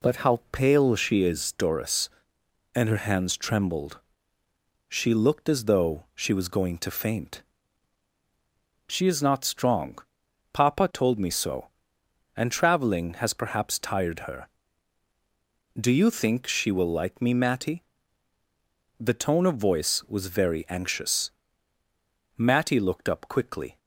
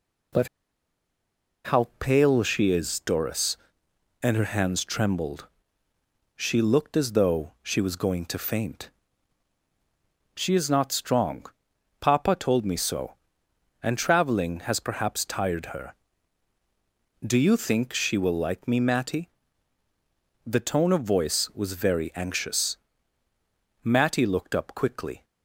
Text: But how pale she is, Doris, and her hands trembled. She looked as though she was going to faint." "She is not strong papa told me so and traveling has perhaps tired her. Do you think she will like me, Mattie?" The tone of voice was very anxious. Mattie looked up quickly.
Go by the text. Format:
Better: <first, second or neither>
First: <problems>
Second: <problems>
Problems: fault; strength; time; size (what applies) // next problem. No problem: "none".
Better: first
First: pauses between "strong" and "papa"; noticeable; at 9.9 s; 0.54 s long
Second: pauses between "But" and "how"; at 0.4 s; 1.1 s long // pauses between "strong" and "papa"; noticeable; at 11.4 s; 0.54 s long